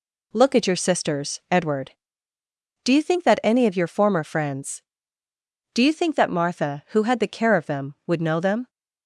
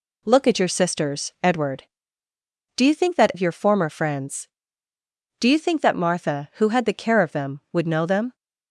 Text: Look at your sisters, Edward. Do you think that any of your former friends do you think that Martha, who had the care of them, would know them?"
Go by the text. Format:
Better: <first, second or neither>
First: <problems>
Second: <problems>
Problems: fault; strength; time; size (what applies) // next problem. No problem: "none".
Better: first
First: none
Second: skips "any"; at 3.3 s